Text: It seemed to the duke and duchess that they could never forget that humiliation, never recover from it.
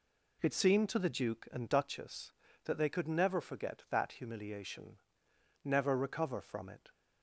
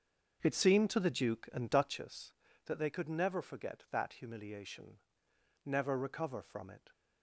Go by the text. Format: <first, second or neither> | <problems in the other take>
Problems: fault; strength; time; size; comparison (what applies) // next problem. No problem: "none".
first | starts louder than the rest; until 2.1 s; 6.5 dB